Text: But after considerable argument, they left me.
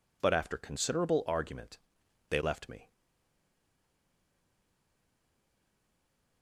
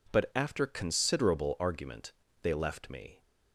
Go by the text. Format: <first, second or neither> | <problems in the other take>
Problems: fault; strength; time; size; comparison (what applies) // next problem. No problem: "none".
second | stays silent after the last word; strong; from 2.9 s on; 3.5 s long